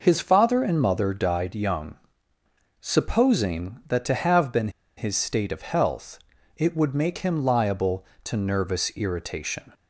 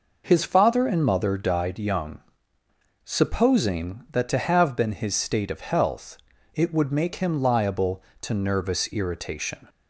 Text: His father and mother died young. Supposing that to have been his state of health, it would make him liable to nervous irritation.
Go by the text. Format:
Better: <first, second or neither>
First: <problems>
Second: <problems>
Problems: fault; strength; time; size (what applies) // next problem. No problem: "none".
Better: second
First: pauses between "been" and "his"; slight; at 4.6 s; 0.27 s long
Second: none